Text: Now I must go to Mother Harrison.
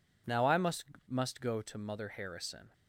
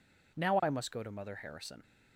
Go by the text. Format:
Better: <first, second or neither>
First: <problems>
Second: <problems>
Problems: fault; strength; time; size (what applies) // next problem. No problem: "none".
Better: second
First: says "must" twice; at 1.0 s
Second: none